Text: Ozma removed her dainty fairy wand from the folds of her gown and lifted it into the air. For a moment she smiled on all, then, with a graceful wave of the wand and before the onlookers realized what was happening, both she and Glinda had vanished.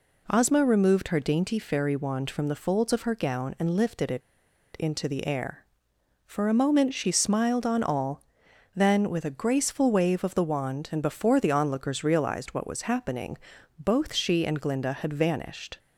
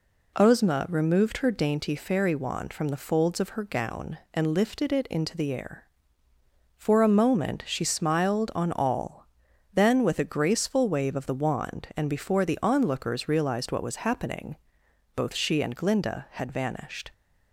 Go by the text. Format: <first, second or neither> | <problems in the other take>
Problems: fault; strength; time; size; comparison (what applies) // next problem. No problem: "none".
second | pauses between "it" and "into"; noticeable; at 4.2 s; 0.57 s long